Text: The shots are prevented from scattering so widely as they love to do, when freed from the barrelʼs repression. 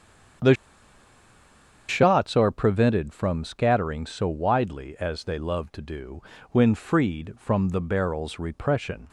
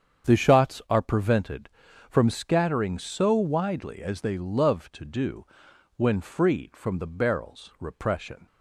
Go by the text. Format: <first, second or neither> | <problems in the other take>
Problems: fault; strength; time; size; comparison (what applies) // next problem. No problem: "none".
second | starts louder than the rest; strong; until 2.7 s; 8 dB; strong in the second // pauses between "The" and "shots"; strong; at 0.5 s; 1.3 s long